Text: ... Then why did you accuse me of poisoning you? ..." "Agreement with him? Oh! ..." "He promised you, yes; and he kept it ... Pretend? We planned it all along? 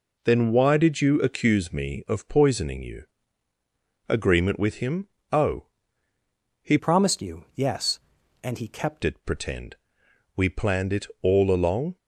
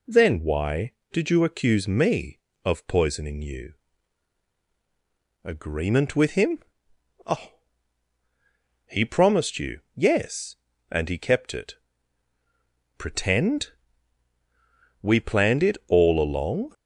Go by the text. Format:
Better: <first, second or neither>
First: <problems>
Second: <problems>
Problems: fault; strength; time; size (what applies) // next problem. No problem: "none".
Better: second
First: changes voice from "promised" to "kept"; from 6.7 to 9.0 s; 2.3 s long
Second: none